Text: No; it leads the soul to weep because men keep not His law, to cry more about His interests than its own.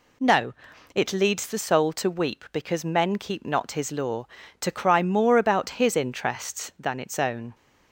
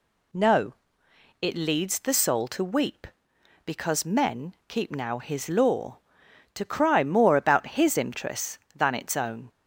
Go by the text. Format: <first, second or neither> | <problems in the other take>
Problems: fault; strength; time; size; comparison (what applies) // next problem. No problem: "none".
first | pauses between "men" and "keep"; slight; at 4.5 s; 0.16 s long // says "now" for "not"; at 4.9 s